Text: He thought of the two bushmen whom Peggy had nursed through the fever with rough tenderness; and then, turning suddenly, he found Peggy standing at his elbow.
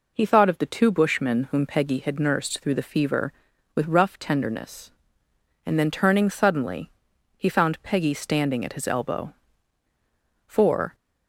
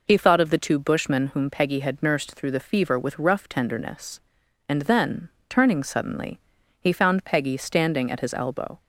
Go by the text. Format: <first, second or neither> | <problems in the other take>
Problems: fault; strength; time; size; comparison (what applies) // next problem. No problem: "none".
second | goes on to say "For"; slight; from 10.4 s on; 0.48 s long